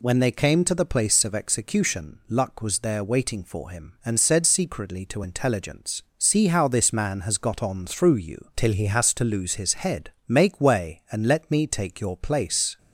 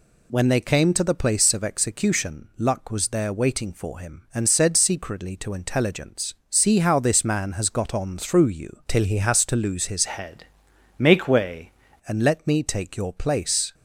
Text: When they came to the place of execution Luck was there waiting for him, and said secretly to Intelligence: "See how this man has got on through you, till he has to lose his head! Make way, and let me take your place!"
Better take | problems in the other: first | changes voice from "head" to "way"; from 10.0 to 11.7 s; 1.7 s long

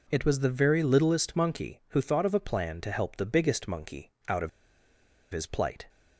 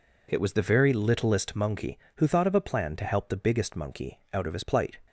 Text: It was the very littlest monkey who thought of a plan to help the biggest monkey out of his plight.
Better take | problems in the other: second | pauses between "monkey" and "out"; slight; at 4.1 s; 0.18 s long // pauses between "of" and "his"; noticeable; at 4.4 s; 0.82 s long

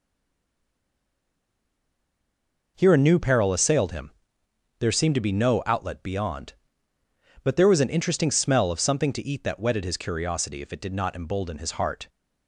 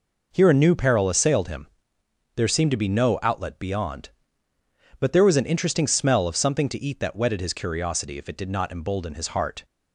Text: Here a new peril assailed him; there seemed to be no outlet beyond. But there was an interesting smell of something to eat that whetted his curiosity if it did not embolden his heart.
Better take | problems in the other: second | stays silent before the first word; strong; until 2.7 s; 2.7 s long

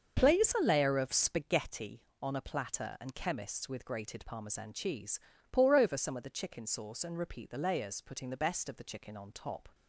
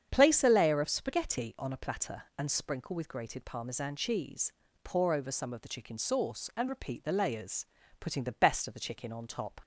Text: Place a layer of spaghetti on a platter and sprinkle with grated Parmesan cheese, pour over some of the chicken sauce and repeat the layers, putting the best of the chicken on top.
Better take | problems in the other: second | starts louder than the rest; until 1.2 s; 6.5 dB; strong in the second // says "chemists" for "sprinkle"; at 3.1 s

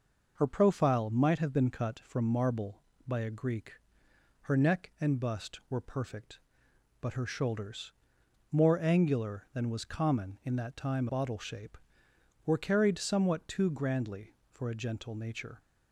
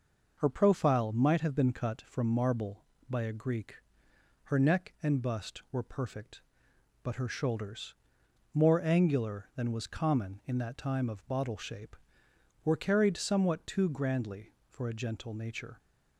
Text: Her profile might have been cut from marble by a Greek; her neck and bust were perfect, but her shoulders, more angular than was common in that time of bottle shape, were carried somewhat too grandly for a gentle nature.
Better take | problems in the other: second | skips "of"; at 11.0 s

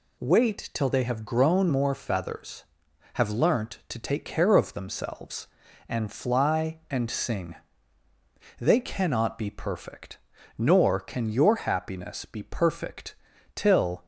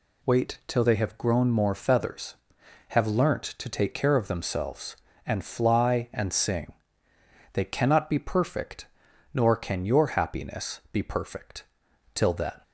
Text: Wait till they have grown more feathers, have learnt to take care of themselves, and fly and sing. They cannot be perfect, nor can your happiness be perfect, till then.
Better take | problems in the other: second | stops before "then"; at 14.0 s

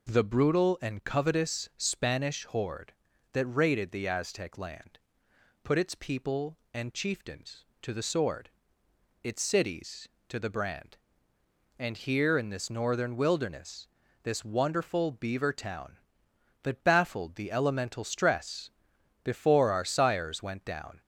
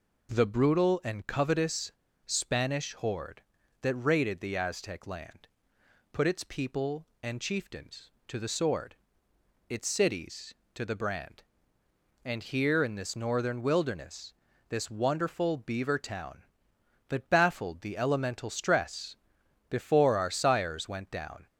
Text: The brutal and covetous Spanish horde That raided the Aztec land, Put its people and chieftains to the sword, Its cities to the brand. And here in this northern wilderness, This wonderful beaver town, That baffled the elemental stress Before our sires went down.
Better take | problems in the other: first | pauses between "covetous" and "Spanish"; slight; at 1.9 s; 0.34 s long // pauses between "stress" and "Before"; noticeable; at 19.1 s; 0.54 s long; noticeable in the first

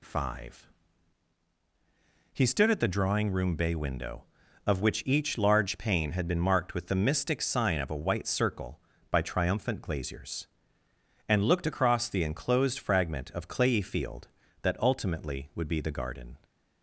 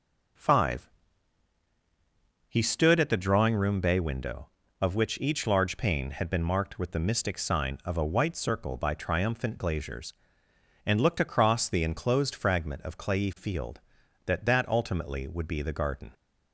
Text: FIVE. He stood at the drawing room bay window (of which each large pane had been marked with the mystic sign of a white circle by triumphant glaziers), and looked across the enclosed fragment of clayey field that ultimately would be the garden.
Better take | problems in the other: first | says "that" twice; at 14.4 s

